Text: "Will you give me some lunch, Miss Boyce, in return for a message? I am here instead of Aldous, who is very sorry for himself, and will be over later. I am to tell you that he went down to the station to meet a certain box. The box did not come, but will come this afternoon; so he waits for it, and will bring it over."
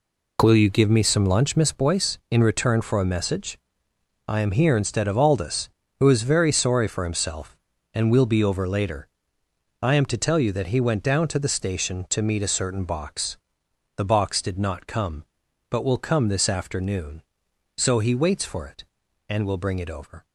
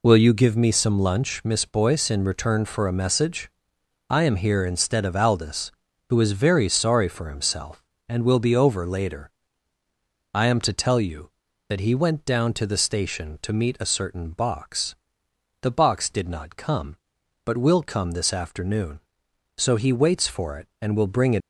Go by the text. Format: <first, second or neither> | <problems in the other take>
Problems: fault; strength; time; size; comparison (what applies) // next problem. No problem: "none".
first | stops before "over"; at 21.4 s